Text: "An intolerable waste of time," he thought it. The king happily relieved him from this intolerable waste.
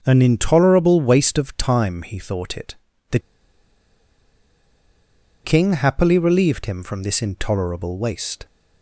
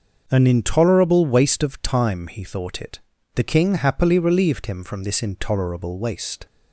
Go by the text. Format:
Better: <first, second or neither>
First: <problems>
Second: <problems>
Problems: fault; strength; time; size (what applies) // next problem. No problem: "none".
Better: second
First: starts louder than the rest; until 1.0 s; 6 dB // pauses between "The" and "king"; strong; at 3.1 s; 2.2 s long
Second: starts louder than the rest; until 1.3 s; 6 dB